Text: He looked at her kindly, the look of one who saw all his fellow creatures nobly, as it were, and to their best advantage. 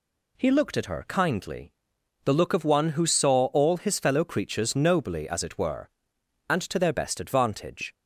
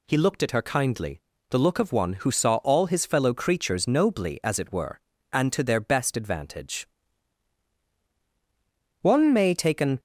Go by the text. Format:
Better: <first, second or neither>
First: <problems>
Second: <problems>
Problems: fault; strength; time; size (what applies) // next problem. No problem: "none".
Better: first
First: none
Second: goes on to say "One may take an"; noticeable; from 9.0 s on; 0.98 s long